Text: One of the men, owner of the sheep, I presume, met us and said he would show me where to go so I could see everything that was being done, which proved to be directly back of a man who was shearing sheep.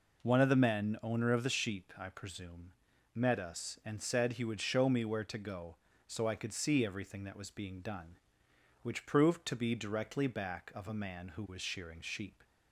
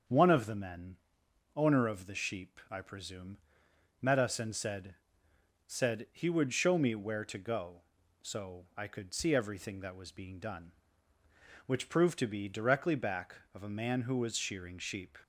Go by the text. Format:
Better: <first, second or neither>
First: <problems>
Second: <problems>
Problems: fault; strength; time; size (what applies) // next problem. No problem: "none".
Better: first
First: none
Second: starts louder than the rest; strong; until 1.6 s; 7 dB // says "said" twice; at 5.6 s